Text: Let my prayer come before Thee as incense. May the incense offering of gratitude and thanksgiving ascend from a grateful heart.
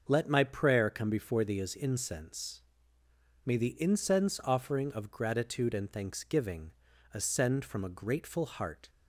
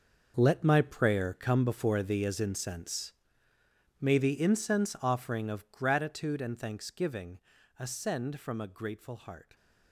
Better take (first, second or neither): first